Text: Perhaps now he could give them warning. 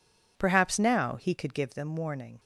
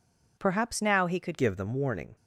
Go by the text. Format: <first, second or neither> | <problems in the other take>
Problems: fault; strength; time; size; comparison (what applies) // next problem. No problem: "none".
first | changes voice at "give"; from 1.3 s on; 0.8 s long